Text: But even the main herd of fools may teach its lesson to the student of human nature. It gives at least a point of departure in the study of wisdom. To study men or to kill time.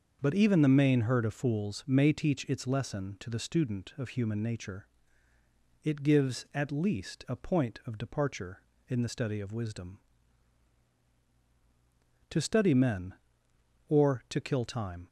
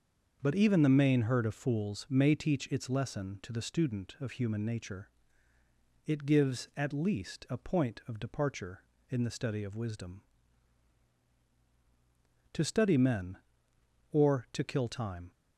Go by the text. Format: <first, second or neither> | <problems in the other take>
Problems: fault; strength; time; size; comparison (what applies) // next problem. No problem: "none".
neither | starts louder than the rest; the same in both